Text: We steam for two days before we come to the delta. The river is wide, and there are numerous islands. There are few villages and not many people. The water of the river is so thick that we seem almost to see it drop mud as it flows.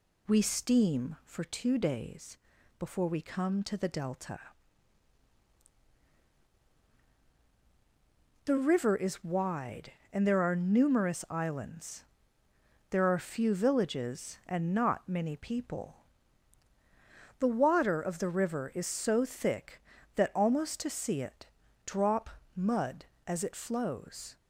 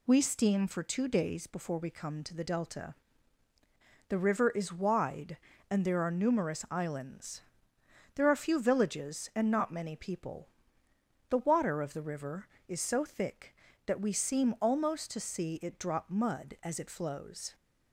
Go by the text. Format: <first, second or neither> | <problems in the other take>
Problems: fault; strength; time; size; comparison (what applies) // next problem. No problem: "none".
second | pauses between "days" and "before"; at 2.3 s; 0.44 s long // skips "we seem"; at 20.3 s // pauses between "it" and "drop"; at 21.4 s; 0.38 s long // pauses between "drop" and "mud"; slight; at 22.2 s; 0.26 s long